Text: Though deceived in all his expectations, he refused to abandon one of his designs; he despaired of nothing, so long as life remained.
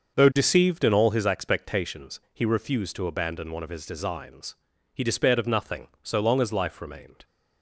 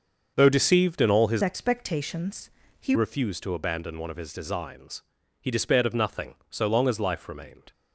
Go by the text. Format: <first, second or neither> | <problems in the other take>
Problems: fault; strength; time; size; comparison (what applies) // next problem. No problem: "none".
first | starts louder than the rest; until 1.3 s; 6.5 dB; also in the first // changes voice from "expectations" to "he"; from 1.4 to 2.9 s; 1.5 s long